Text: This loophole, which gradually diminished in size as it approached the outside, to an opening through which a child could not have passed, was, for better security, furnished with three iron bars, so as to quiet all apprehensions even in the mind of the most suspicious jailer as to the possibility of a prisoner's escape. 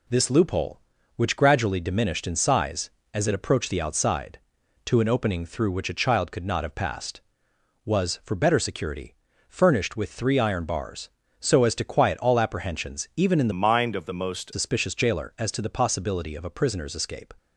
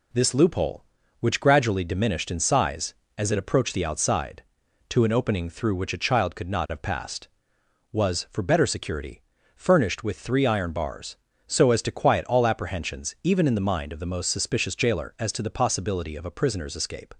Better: second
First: changes voice from "mind" to "most"; from 13.5 to 14.5 s; 1.0 s long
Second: none

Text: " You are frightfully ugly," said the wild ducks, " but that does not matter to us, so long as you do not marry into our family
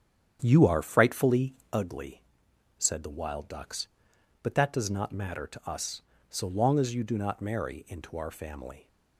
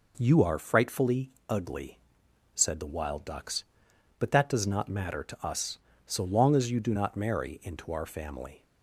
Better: second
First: starts louder than the rest; strong; until 1.9 s; 8 dB // pauses between "frightfully" and "ugly"; slight; at 1.5 s; 0.20 s long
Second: pauses between "frightfully" and "ugly"; slight; at 1.2 s; 0.20 s long

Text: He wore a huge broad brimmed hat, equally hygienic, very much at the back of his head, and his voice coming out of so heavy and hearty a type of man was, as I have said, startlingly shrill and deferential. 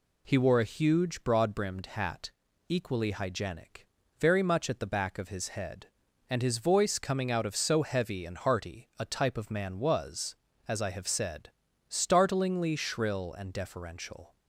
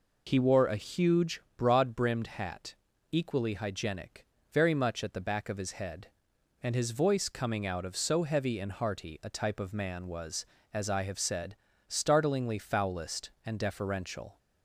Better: first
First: none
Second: pauses between "huge" and "broad"; slight; at 1.3 s; 0.16 s long // says "foulest" for "shrill"; at 12.5 s

